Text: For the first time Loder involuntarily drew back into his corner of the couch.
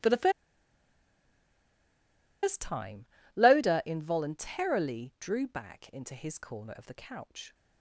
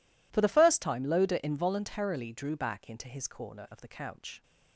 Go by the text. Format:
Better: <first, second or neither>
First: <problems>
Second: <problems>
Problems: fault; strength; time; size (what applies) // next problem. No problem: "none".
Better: second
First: pauses between "the" and "first"; strong; at 0.2 s; 2.1 s long // pauses between "time" and "Loder"; slight; at 3.0 s; 0.30 s long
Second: none